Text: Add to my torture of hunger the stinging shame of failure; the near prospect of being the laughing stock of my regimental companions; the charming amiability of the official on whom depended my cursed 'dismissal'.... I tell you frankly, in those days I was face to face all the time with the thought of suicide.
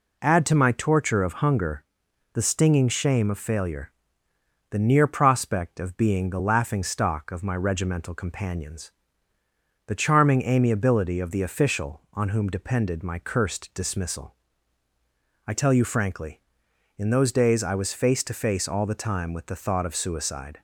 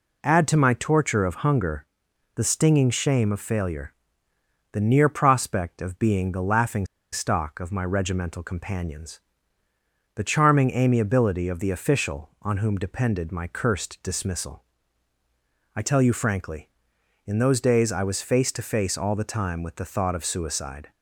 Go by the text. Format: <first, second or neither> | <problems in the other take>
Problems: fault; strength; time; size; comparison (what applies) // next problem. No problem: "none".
first | pauses between "hunger" and "the"; noticeable; at 1.8 s; 0.50 s long; noticeable in the first // pauses between "laughing" and "stock"; slight; at 6.8 s; 0.27 s long